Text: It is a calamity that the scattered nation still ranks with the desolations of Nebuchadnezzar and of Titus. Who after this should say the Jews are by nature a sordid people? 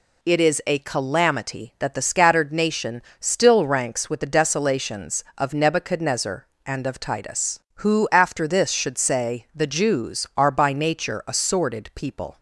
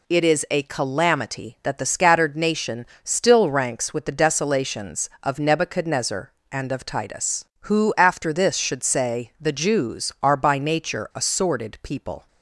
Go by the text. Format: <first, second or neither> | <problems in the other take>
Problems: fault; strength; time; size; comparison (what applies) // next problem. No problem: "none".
neither | pauses between "nation" and "still"; slight; the same in both